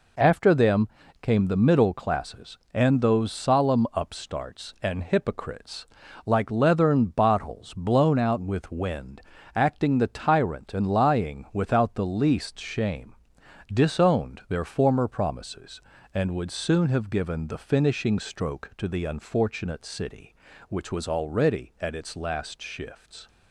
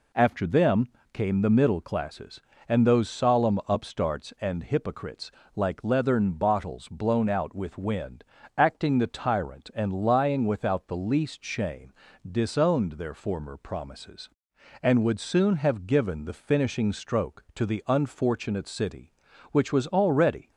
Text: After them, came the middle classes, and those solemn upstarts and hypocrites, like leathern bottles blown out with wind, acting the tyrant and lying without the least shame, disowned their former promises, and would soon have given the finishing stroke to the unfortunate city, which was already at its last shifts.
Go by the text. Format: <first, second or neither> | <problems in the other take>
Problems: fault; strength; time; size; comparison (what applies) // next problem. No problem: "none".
first | stops before "at its last shifts"; at 20.5 s